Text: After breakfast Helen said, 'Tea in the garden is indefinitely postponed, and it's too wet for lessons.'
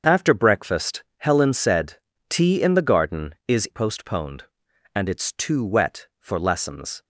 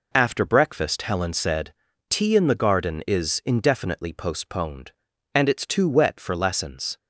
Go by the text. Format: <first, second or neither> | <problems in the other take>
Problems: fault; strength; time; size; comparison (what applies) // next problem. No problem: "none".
second | starts louder than the rest; until 1.1 s; 7 dB // skips "indefinitely"; at 3.6 s